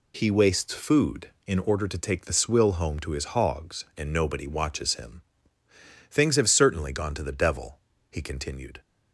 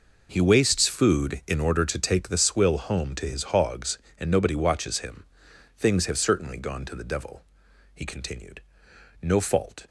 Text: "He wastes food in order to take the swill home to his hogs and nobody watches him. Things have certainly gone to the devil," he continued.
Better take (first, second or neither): first